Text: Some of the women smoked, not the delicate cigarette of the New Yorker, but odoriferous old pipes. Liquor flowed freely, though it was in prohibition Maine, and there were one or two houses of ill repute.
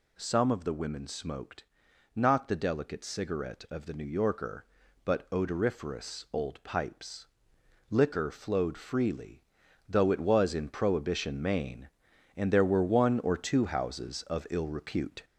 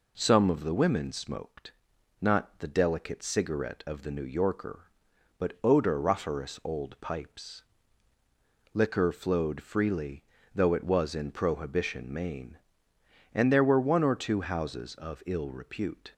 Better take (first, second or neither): second